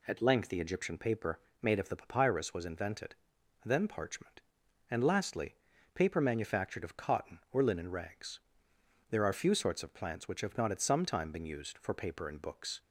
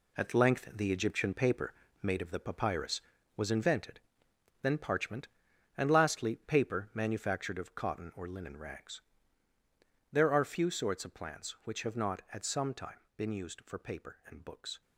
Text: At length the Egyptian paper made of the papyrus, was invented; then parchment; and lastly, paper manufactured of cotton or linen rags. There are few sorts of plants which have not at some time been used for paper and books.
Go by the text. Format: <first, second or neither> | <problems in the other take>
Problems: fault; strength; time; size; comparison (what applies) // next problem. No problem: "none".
first | gets quieter; strong; throughout; 9 dB // pauses between "paper" and "made"; slight; at 1.7 s; 0.30 s long; slight in the first // pauses between "time" and "been"; slight; at 12.9 s; 0.16 s long